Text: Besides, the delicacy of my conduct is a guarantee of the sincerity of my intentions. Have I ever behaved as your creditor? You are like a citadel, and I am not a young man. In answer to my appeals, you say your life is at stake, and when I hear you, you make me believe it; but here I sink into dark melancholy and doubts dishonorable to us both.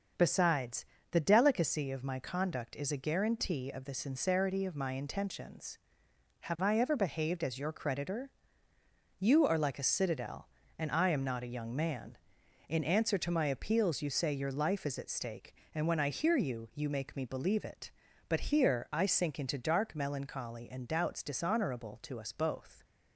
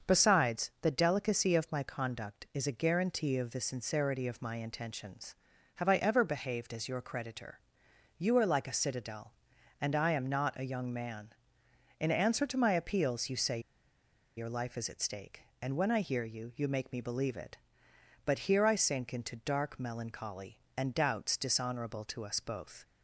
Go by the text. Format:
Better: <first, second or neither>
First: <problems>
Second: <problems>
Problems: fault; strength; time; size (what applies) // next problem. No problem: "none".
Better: first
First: starts louder than the rest; noticeable; until 1.4 s; 6 dB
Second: starts louder than the rest; until 1.1 s; 6.5 dB // pauses between "say" and "your"; noticeable; at 13.5 s; 0.77 s long